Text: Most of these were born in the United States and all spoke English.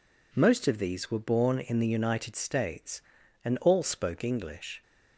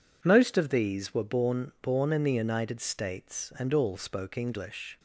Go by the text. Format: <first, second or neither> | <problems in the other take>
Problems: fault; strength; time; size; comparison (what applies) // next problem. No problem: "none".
first | says "born" twice; at 1.8 s